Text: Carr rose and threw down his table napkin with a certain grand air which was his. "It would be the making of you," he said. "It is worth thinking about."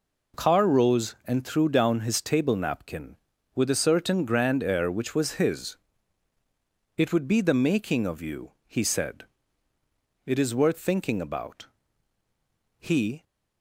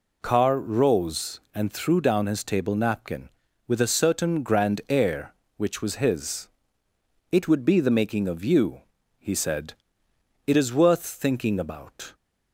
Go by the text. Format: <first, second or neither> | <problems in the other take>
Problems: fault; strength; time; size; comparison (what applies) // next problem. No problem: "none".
second | goes on to say "He"; slight; from 12.7 s on; 0.44 s long